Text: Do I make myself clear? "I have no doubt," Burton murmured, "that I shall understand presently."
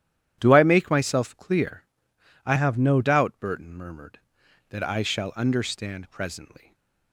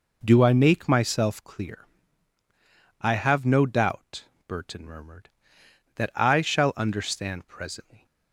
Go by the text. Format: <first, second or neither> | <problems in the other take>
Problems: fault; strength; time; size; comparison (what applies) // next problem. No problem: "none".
second | starts louder than the rest; strong; until 1.4 s; 11 dB // changes voice from "have" to "no"; from 2.5 to 3.0 s; 0.5 s long // stays silent after the last word; slight; from 6.5 s on; 0.6 s long